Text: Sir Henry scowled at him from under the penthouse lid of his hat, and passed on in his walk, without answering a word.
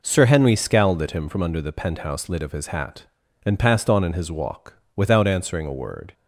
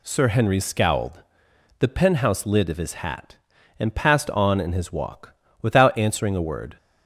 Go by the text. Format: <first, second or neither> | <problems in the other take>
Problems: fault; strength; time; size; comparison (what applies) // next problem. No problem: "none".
first | skips "at him from under"; at 1.5 s